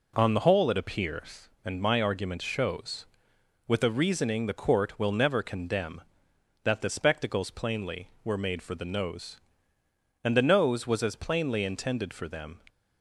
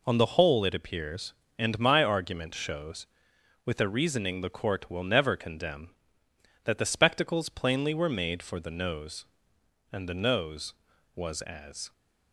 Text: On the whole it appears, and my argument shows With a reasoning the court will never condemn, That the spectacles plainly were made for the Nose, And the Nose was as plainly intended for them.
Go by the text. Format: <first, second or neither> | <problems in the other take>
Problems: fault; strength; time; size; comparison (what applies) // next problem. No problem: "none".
first | stops before "plainly intended for them"; at 11.9 s